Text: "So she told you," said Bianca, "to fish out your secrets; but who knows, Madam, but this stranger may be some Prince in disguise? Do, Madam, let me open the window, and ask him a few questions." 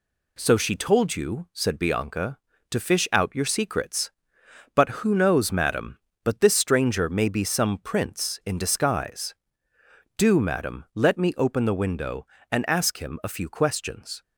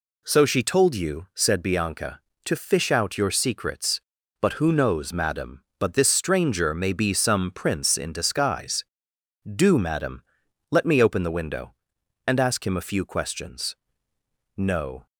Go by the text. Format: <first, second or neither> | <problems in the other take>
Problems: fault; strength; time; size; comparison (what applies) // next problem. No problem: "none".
first | goes on to say "No"; from 14.5 s on; 0.50 s long